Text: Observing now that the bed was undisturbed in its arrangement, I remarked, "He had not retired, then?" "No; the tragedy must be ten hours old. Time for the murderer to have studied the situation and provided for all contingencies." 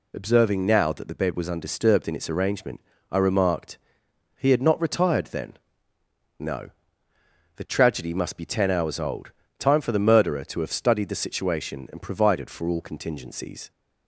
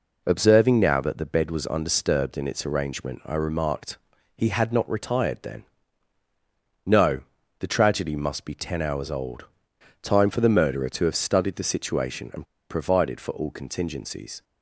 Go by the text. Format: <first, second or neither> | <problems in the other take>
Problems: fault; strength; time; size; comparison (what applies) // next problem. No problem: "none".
first | pauses between "and" and "provided"; slight; at 12.4 s; 0.24 s long